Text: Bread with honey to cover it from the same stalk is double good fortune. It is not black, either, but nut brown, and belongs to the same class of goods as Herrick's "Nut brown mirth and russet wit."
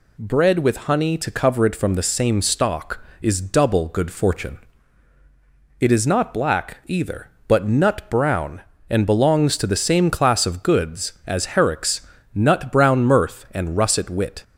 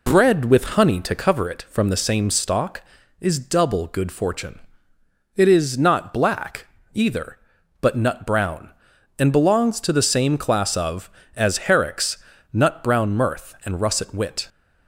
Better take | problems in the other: first | skips "goods"; at 11.2 s // pauses between "Herrick's" and "Nut"; slight; at 12.2 s; 0.30 s long; slight in the first

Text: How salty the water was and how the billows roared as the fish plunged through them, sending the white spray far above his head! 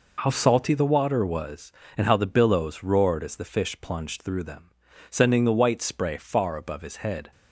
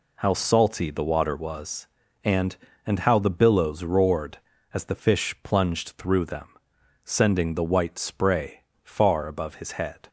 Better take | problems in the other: first | says "and" twice; at 2.8 s // pauses between "spray" and "far"; slight; at 8.6 s; 0.22 s long

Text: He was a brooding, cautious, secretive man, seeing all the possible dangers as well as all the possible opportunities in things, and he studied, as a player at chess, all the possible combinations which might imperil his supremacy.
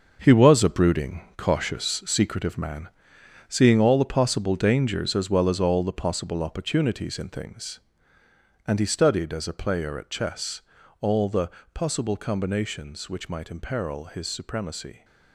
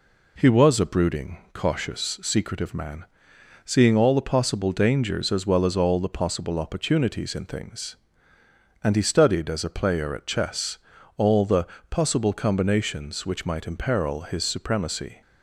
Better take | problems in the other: second | gets quieter; strong; throughout; 10 dB // pauses between "the" and "possible"; slight; at 11.4 s; 0.24 s long; slight in the second

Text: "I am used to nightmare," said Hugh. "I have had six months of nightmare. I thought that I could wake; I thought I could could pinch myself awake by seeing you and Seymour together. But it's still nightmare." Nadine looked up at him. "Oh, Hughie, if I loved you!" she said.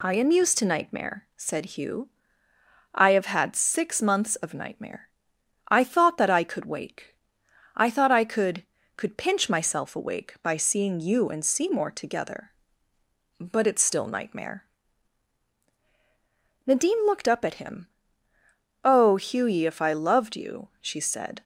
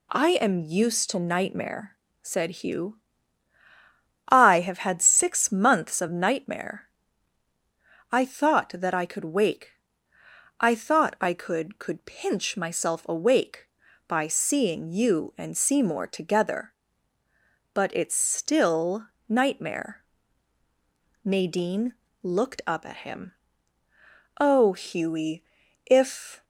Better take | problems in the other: first | pauses between "still" and "nightmare"; slight; at 19.0 s; 0.20 s long // pauses between "Nadine" and "looked"; slight; at 21.9 s; 0.28 s long // stops before "I loved you she said"; at 26.4 s

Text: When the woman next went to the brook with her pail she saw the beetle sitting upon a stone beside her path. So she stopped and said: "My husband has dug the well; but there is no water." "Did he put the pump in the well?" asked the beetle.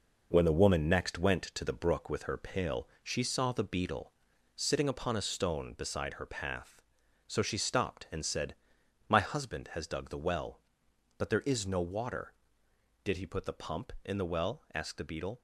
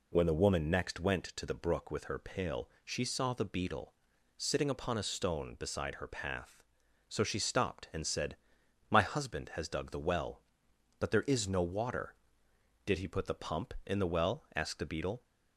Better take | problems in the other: second | gets quieter; throughout; 6.5 dB // pauses between "pail" and "she"; slight; at 2.8 s; 0.16 s long; slight in the second // pauses between "beetle" and "sitting"; at 4.1 s; 0.42 s long; also in the second

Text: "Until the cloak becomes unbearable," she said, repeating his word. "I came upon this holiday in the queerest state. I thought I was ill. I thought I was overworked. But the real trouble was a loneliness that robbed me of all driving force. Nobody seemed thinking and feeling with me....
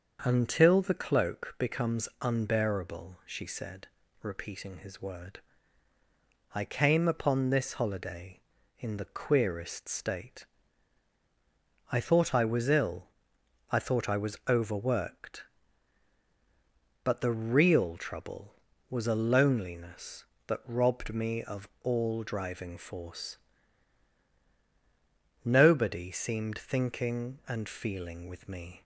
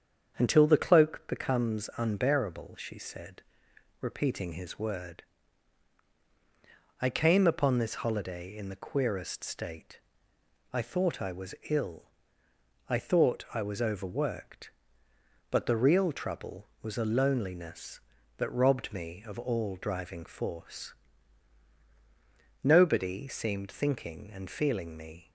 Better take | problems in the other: first | starts louder than the rest; strong; until 1.3 s; 7.5 dB; also in the first // pauses between "was" and "ill"; slight; at 11.5 s; 0.16 s long // skips "with"; at 24.9 s

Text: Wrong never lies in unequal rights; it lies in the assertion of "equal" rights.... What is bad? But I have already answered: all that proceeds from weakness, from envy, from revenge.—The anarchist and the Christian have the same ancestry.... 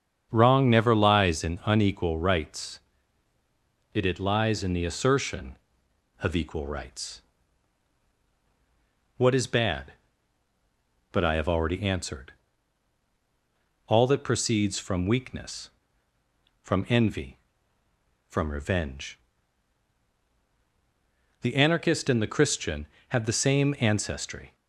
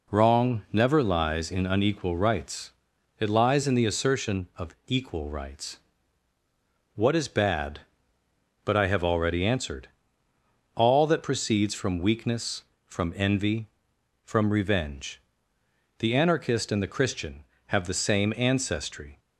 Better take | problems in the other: second | starts louder than the rest; strong; until 1.3 s; 7.5 dB // says "it" twice; at 4.0 s

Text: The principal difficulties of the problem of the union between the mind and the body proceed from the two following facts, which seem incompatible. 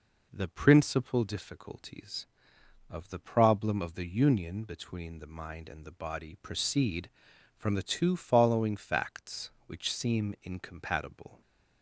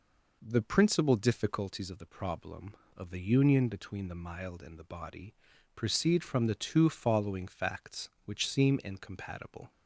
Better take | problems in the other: first | says "mild" for "mind"; at 4.2 s // pauses between "body" and "proceed"; at 5.3 s; 0.40 s long

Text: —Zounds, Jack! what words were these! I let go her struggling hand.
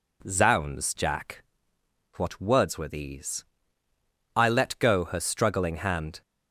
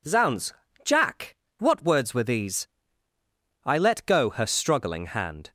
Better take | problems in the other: neither | none

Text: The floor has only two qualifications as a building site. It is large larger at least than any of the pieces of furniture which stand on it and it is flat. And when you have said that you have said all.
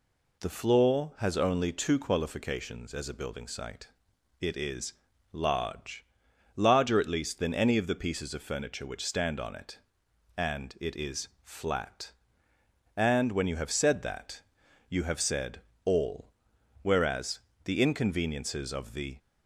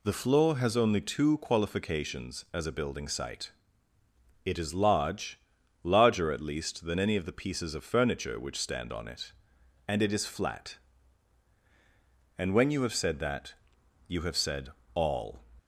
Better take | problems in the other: second | pauses between "is" and "large"; at 4.9 s; 0.40 s long // pauses between "large" and "larger"; noticeable; at 6.0 s; 0.54 s long; noticeable in the second // pauses between "that" and "you"; noticeable; at 14.4 s; 0.48 s long; noticeable in the second // pauses between "said" and "all"; slight; at 15.6 s; 0.24 s long; slight in the second // goes on to say "Whereas the inconveniences of the"; strong; from 16.8 s on; 2.3 s long

